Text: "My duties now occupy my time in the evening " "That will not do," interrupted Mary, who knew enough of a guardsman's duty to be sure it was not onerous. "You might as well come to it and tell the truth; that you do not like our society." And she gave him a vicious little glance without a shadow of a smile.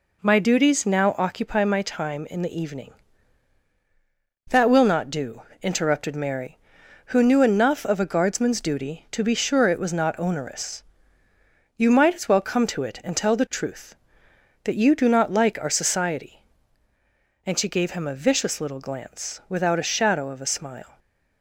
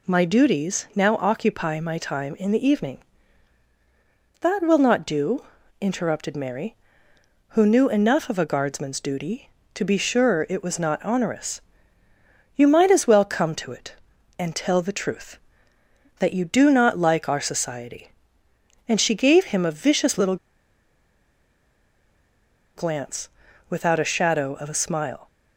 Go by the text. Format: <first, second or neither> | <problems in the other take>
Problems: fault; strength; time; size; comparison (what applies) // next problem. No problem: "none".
first | pauses between "little" and "glance"; strong; at 20.3 s; 2.4 s long // pauses between "glance" and "without"; at 23.2 s; 0.40 s long